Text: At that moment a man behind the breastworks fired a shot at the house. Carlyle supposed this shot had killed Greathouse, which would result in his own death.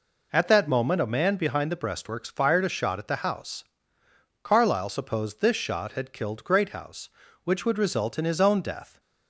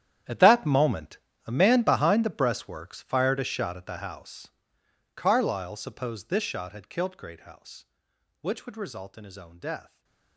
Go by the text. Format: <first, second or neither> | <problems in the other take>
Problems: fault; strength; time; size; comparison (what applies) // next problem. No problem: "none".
first | gets quieter; strong; throughout; 18.5 dB // pauses between "moment" and "a"; slight; at 1.1 s; 0.30 s long // stays silent after the last word; slight; from 9.8 s on; 0.5 s long